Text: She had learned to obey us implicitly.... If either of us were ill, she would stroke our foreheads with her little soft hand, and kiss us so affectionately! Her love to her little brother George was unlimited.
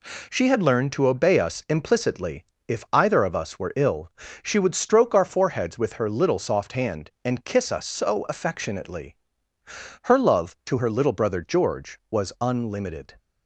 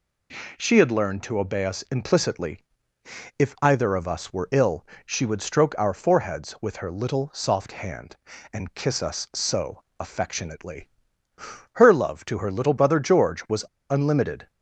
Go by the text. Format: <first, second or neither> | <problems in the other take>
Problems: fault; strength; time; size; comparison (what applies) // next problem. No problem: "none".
first | pauses between "so" and "affectionately"; slight; at 9.8 s; 0.16 s long // pauses between "was" and "unlimited"; slight; at 13.6 s; 0.24 s long